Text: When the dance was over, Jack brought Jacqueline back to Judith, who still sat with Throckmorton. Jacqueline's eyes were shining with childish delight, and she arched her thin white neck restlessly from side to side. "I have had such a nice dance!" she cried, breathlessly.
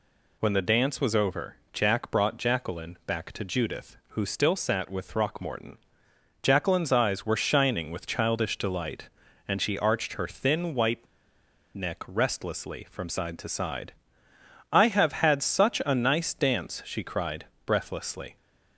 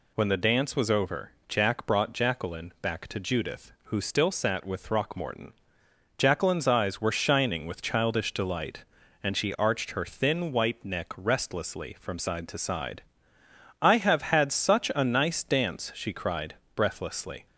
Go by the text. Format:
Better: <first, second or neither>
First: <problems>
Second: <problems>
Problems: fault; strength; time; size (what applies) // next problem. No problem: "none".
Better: second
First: pauses between "white" and "neck"; noticeable; at 11.0 s; 0.68 s long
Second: none